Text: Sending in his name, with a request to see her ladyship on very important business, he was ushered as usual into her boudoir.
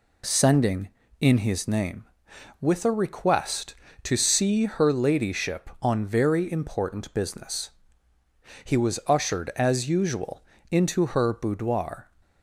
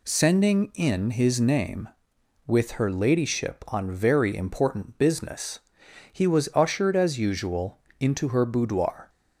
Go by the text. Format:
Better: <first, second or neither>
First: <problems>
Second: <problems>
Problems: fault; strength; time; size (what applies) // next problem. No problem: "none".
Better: first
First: pauses between "usual" and "into"; slight; at 10.4 s; 0.28 s long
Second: skips "a request to see"; at 2.7 s // pauses between "usual" and "into"; slight; at 7.7 s; 0.24 s long